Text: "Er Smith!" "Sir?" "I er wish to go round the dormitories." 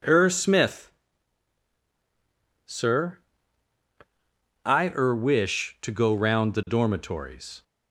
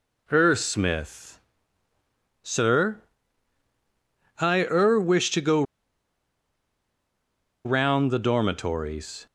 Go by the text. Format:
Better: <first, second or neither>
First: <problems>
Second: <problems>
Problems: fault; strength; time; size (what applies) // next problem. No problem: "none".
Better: first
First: none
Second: pauses between "go" and "round"; strong; at 5.6 s; 2.0 s long